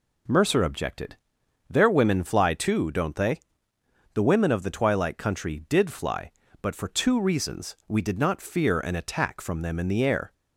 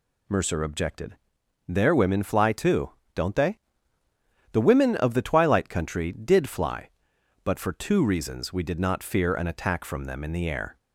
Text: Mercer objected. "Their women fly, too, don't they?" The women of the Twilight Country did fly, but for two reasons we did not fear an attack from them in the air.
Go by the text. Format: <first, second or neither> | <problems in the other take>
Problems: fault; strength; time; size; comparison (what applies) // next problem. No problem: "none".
neither | none